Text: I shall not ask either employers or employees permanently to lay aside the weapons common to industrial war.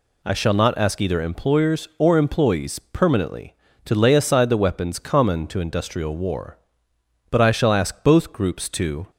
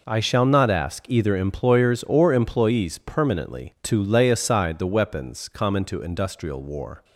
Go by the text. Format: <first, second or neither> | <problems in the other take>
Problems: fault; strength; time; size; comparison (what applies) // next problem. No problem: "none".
second | goes on to say "But I shall ask both groups to"; strong; from 7.3 s on; 1.8 s long